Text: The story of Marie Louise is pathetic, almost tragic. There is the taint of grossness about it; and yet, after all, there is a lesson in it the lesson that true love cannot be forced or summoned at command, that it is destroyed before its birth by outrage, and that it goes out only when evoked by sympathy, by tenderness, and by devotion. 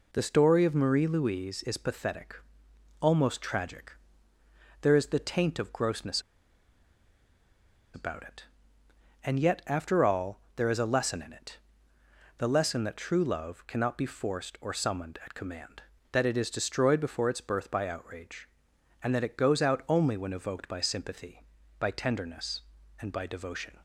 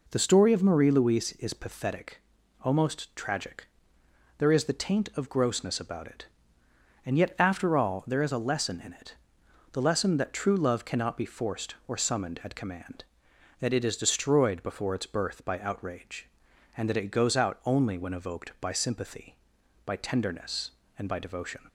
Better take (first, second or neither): second